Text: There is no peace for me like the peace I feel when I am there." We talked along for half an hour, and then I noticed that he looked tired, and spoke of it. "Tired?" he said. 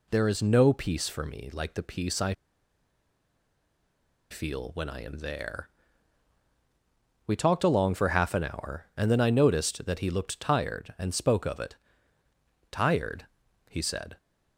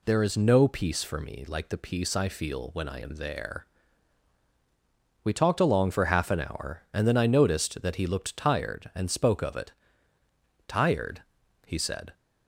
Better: second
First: pauses between "I" and "feel"; strong; at 2.3 s; 1.9 s long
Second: none

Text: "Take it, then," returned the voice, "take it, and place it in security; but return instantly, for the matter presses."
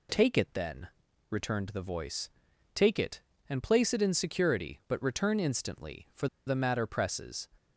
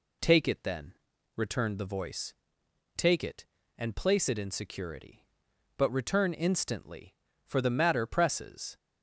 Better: second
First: pauses between "for" and "the"; slight; at 6.2 s; 0.20 s long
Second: none

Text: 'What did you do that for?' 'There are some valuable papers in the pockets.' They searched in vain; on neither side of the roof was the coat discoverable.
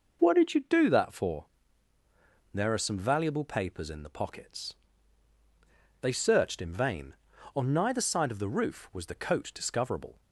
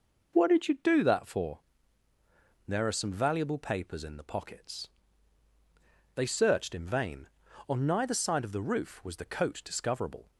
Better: neither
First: none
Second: none

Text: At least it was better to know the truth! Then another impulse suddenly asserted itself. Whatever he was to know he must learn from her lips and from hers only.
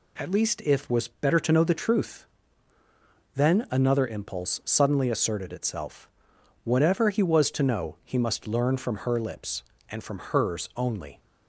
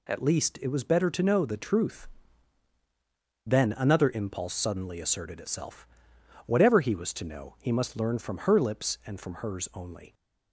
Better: second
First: says "if" for "it"; at 0.6 s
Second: none

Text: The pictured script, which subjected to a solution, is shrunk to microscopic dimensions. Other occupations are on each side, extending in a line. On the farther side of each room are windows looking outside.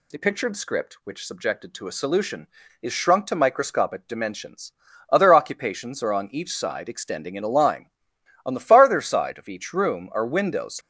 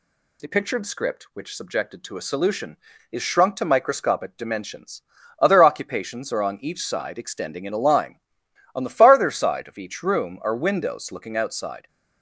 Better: second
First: stops before "looking outside"; at 10.8 s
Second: none

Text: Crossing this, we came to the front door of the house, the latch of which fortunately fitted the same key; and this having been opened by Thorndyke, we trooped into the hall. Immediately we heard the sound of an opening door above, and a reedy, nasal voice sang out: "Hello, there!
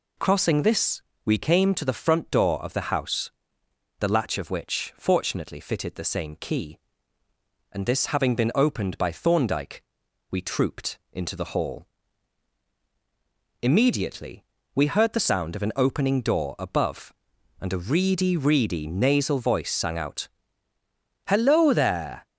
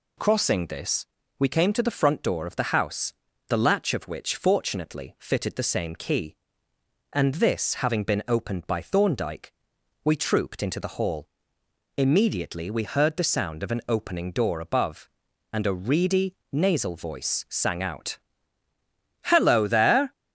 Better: second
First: pauses between "Immediately" and "we"; slight; at 14.4 s; 0.30 s long // says "reedy" twice; at 18.3 s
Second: none

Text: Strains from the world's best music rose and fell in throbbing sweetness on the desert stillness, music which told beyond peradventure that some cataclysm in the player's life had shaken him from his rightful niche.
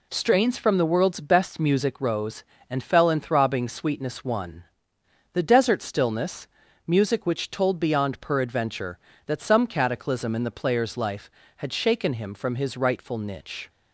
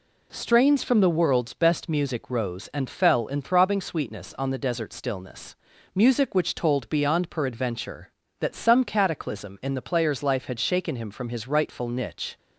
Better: second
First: says "one" for "on"; at 4.2 s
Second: none

